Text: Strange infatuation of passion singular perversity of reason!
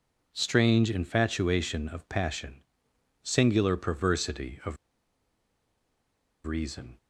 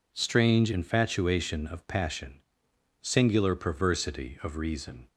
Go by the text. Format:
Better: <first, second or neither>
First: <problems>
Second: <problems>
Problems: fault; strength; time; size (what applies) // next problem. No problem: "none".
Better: second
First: pauses between "passion" and "singular"; noticeable; at 2.6 s; 0.60 s long // pauses between "of" and "reason"; strong; at 4.7 s; 1.7 s long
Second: pauses between "passion" and "singular"; noticeable; at 2.3 s; 0.60 s long